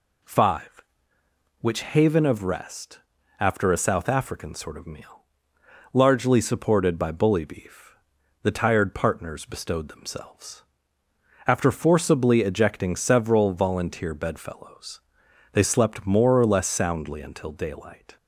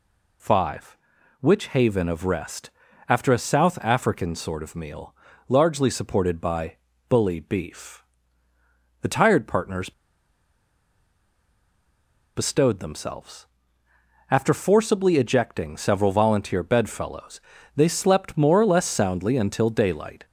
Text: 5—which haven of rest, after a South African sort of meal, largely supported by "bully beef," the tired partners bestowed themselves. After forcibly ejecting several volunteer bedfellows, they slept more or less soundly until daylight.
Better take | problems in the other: first | pauses between "by" and "bully"; slight; at 6.7 s; 0.32 s long // pauses between "partners" and "bestowed"; strong; at 9.9 s; 2.4 s long

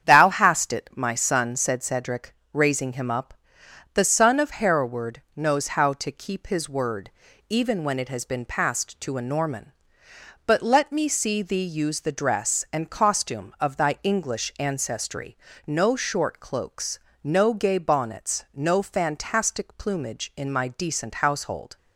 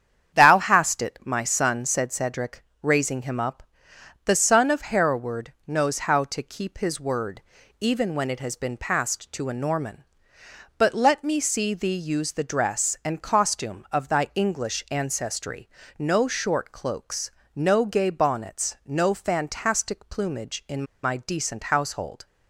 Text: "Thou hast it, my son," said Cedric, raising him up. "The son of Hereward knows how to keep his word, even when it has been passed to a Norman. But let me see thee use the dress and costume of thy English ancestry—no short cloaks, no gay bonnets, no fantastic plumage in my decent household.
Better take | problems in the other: first | starts louder than the rest; strong; until 1.4 s; 8.5 dB; strong in the first // pauses between "in" and "my"; slight; at 20.8 s; 0.18 s long

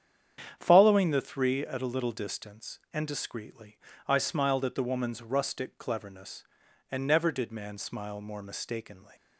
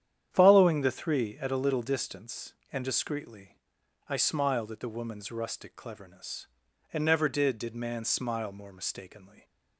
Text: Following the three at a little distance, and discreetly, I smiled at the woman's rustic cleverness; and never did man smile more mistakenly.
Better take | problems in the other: first | starts louder than the rest; strong; until 1.3 s; 9.5 dB; strong in the first // says "did" twice; at 7.5 s

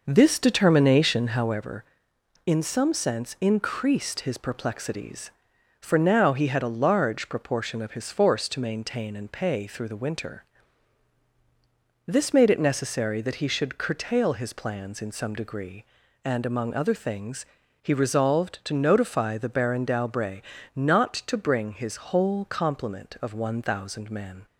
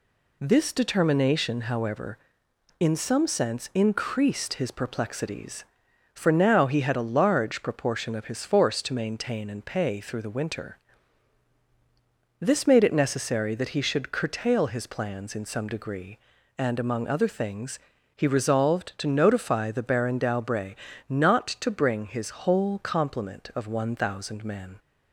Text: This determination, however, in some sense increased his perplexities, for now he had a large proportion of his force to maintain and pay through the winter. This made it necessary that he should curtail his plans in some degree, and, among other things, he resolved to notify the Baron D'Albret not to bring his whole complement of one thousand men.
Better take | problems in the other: second | starts louder than the rest; noticeable; until 1.6 s; 5.5 dB // pauses between "D'Albret" and "not"; slight; at 20.4 s; 0.34 s long; slight in the second

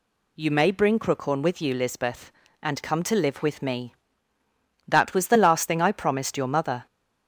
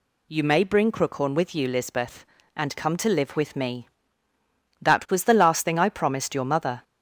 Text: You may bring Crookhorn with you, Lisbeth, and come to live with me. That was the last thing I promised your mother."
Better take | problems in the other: neither | none

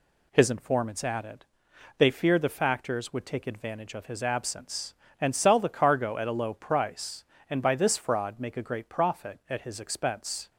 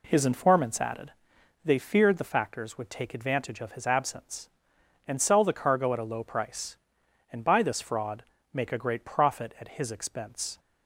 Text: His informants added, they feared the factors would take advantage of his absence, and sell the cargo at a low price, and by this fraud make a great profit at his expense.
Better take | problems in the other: first | starts louder than the rest; slight; until 1.7 s; 2.5 dB // pauses between "fraud" and "make"; slight; at 8.2 s; 0.30 s long

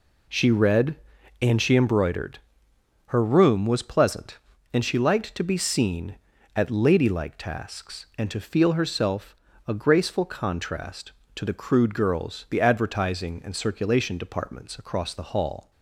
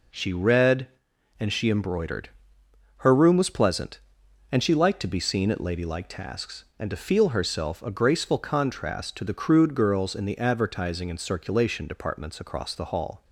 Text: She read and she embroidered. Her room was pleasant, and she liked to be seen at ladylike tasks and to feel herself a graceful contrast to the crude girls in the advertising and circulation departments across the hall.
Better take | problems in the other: second | pauses between "herself" and "a"; slight; at 9.3 s; 0.32 s long // skips "in"; at 12.4 s

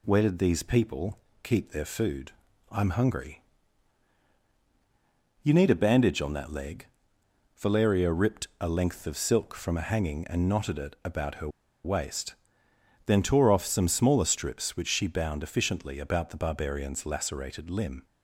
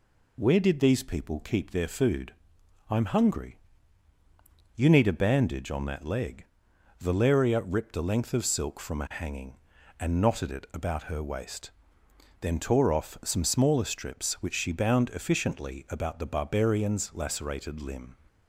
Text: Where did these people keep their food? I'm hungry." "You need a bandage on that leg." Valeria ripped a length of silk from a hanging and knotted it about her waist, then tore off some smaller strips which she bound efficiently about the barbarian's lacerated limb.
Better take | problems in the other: second | pauses between "people" and "keep"; slight; at 1.1 s; 0.24 s long // pauses between "her" and "waist"; slight; at 11.4 s; 0.35 s long

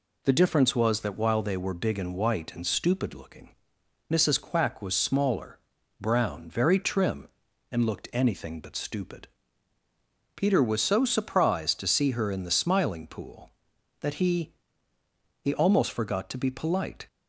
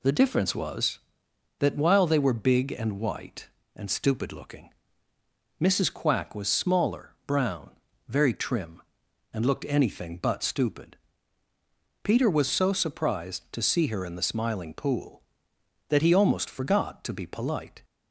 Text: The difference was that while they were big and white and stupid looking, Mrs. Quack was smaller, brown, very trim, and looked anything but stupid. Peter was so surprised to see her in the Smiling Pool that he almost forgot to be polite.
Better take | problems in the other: second | says "he" twice; at 15.4 s

